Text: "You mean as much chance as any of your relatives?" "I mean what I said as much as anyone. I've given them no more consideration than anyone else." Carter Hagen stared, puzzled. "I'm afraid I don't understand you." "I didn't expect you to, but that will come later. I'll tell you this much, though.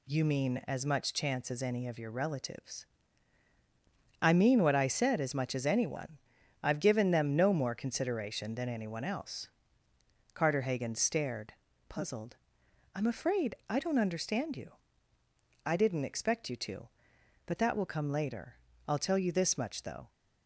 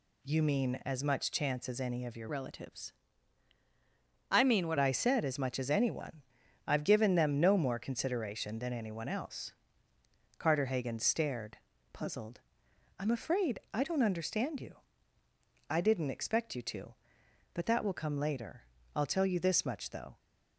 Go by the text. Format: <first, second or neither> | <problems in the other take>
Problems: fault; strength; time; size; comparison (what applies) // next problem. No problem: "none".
first | changes voice from "relatives" to "what"; from 2.2 to 4.7 s; 2.5 s long // pauses between "afraid" and "I"; slight; at 13.5 s; 0.16 s long; slight in the first